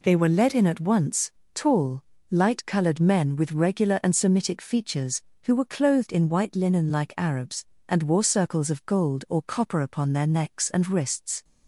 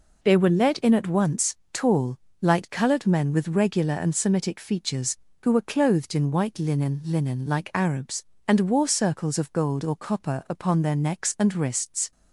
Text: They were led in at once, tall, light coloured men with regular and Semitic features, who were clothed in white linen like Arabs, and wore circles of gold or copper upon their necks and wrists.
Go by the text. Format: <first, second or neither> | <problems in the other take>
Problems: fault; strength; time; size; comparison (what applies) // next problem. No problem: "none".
first | says "linen" twice; at 7.0 s